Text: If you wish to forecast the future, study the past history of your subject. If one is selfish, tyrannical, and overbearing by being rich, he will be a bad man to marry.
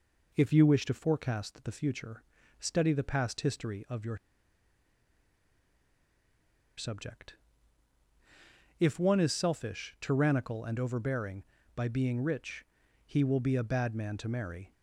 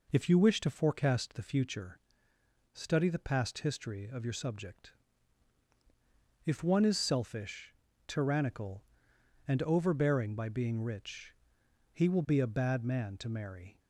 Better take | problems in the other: second | pauses between "your" and "subject"; strong; at 4.1 s; 2.6 s long

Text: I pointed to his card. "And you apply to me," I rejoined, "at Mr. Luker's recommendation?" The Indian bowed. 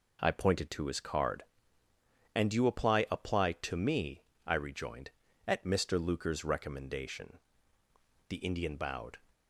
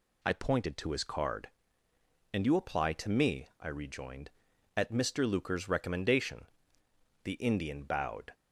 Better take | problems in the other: second | says "apply" twice; at 3.0 s

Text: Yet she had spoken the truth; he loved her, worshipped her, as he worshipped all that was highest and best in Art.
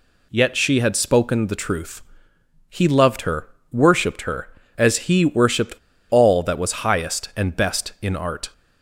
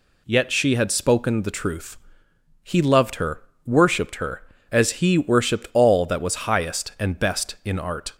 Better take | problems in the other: second | pauses between "worshipped" and "all"; slight; at 5.7 s; 0.35 s long

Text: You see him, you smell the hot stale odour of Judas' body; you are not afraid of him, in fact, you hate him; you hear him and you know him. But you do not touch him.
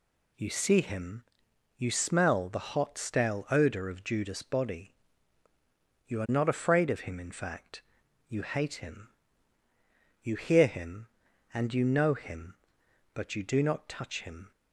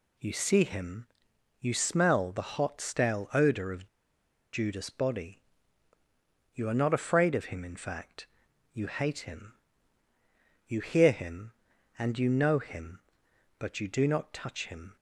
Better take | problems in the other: first | pauses between "of" and "Judas"; noticeable; at 3.8 s; 0.65 s long

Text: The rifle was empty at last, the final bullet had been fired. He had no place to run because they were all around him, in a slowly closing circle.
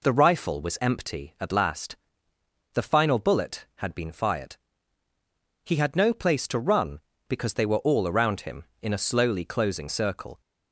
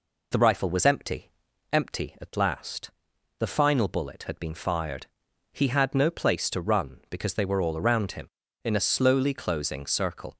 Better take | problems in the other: first | says "empty" twice; at 1.7 s

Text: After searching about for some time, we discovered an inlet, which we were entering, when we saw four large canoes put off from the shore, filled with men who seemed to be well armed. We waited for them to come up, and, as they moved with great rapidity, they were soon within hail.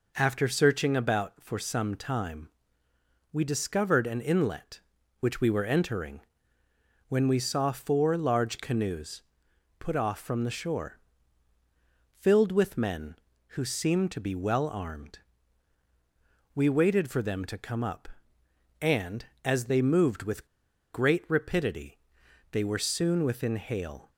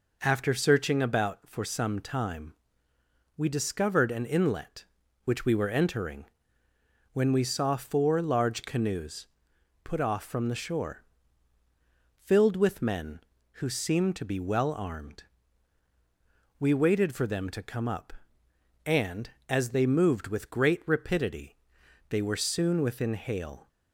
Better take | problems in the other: second | pauses between "canoes" and "put"; noticeable; at 9.2 s; 0.58 s long; noticeable in the second // pauses between "with" and "great"; noticeable; at 20.4 s; 0.46 s long

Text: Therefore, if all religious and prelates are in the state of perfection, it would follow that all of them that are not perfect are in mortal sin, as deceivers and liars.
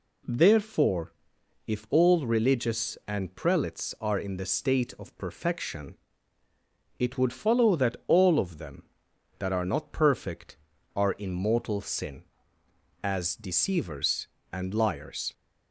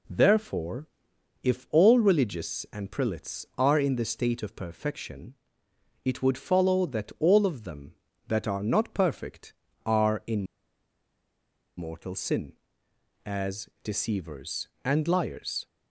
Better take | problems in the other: first | pauses between "in" and "mortal"; strong; at 10.4 s; 1.3 s long

